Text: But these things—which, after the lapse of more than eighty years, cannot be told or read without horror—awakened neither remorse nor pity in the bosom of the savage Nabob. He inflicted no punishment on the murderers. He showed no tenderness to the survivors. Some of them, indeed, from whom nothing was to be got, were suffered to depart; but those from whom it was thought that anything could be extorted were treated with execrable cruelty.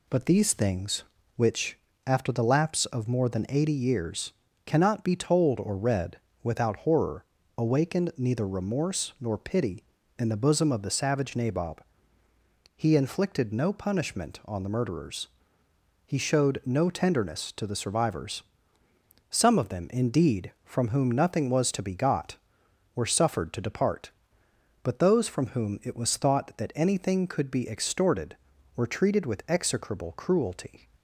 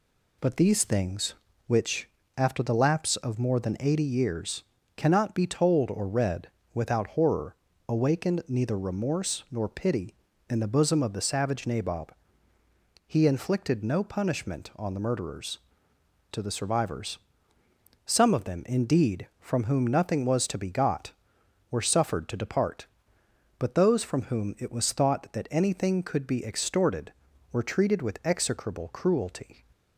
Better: first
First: pauses between "read" and "without"; slight; at 6.1 s; 0.26 s long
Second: pauses between "read" and "without"; slight; at 6.4 s; 0.26 s long // skips "He showed no tenderness"; at 15.9 s

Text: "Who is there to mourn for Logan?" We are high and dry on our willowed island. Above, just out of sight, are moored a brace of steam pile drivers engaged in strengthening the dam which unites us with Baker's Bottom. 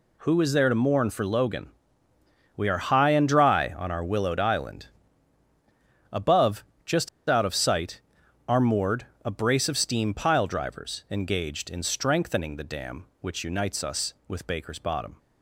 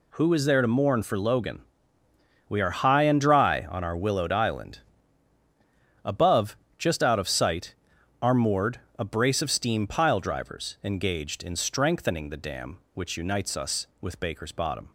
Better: second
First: pauses between "just" and "out"; slight; at 7.0 s; 0.20 s long // pauses between "moored" and "a"; slight; at 9.0 s; 0.18 s long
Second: pauses between "moored" and "a"; slight; at 8.7 s; 0.18 s long

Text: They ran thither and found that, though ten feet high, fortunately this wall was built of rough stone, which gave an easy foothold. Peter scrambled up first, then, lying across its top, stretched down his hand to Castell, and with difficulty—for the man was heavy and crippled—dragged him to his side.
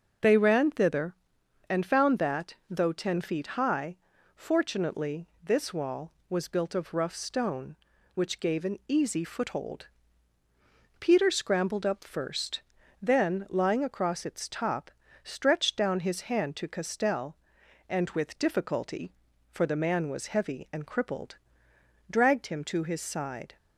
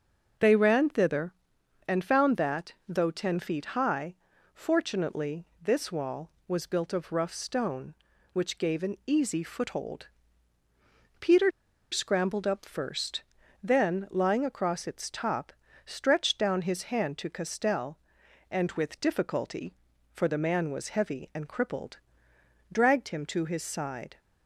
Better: first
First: starts louder than the rest; until 1.7 s; 6.5 dB // pauses between "fortunately" and "this"; slight; at 5.2 s; 0.16 s long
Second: starts louder than the rest; until 1.9 s; 6.5 dB // pauses between "fortunately" and "this"; slight; at 5.4 s; 0.16 s long // pauses between "Peter" and "scrambled"; at 11.4 s; 0.42 s long

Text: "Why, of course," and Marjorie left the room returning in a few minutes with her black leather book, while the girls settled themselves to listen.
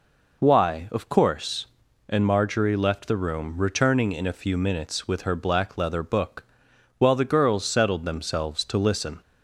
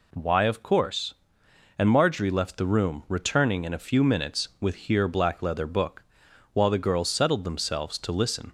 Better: first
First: none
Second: says "here" for "her"; at 4.7 s

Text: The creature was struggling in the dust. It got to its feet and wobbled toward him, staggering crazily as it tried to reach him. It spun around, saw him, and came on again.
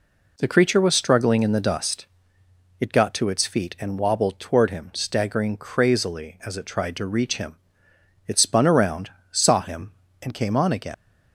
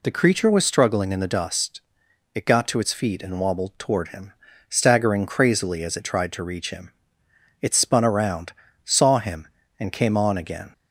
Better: second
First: leaves "again" unfinished; at 10.9 s; 95 ms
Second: none

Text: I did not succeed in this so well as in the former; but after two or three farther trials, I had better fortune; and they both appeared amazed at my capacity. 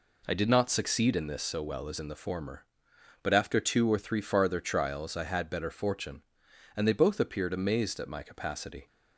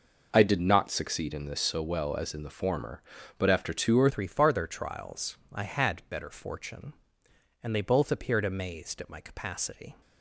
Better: first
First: none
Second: changes voice at "three"; from 4.0 s on; 5.9 s long

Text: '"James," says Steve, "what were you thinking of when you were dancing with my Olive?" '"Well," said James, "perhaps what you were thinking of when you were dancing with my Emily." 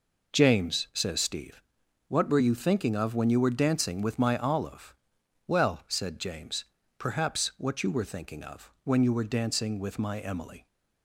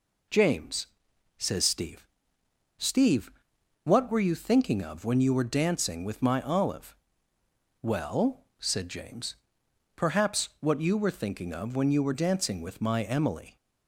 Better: first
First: none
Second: says "Steve" twice; at 2.7 s

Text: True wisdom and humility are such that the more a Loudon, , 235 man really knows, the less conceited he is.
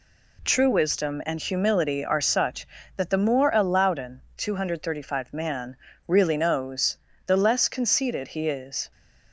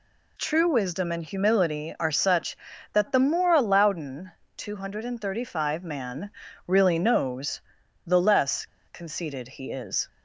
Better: first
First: pauses between "man" and "really"; slight; at 5.7 s; 0.32 s long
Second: pauses between "man" and "really"; at 6.2 s; 0.38 s long // pauses between "less" and "conceited"; slight; at 8.6 s; 0.21 s long

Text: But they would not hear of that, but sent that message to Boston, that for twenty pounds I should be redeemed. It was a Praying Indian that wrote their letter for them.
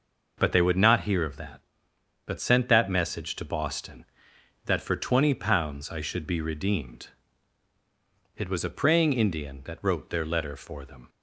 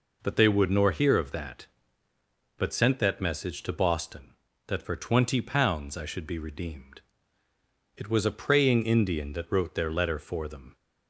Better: first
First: none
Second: says "nor" for "not"; at 0.6 s

